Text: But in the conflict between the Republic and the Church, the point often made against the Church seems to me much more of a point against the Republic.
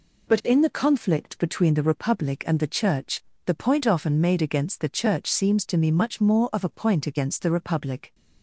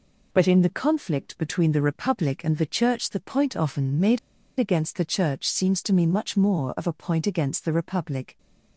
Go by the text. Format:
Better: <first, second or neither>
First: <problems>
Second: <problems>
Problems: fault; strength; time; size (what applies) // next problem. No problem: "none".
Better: first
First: none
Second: pauses between "made" and "against"; at 4.1 s; 0.40 s long